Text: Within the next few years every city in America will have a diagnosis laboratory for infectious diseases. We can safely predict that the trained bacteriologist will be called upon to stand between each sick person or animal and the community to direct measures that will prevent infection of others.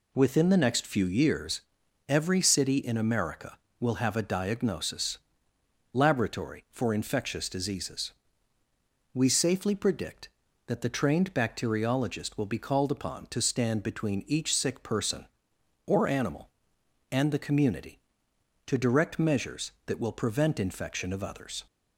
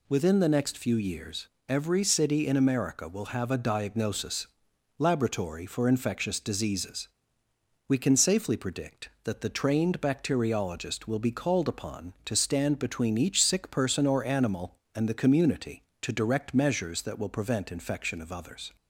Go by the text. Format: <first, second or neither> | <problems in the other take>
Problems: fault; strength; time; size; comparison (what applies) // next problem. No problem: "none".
second | pauses between "years" and "every"; noticeable; at 1.5 s; 0.48 s long; slight in the second // pauses between "diagnosis" and "laboratory"; noticeable; at 5.1 s; 0.76 s long; noticeable in the second // skips "can"; at 9.2 s